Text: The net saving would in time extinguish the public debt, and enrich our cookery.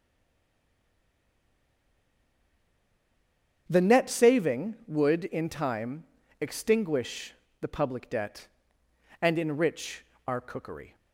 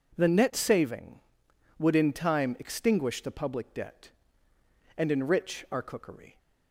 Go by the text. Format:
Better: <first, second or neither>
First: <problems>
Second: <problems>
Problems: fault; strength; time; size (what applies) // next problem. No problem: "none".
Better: second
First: stays silent before the first word; strong; until 3.6 s; 3.6 s long // starts louder than the rest; strong; until 4.6 s; 8 dB // pauses between "time" and "extinguish"; slight; at 6.0 s; 0.36 s long // pauses between "extinguish" and "the"; slight; at 7.3 s; 0.28 s long // pauses between "enrich" and "our"; slight; at 10.0 s; 0.22 s long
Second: none